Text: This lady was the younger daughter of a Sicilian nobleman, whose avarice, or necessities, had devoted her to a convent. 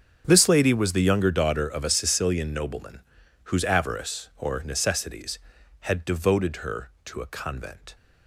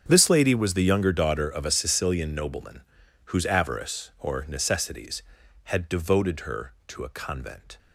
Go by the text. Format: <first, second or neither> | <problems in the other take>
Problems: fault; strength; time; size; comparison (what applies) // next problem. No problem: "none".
neither | starts louder than the rest; strong; the same in both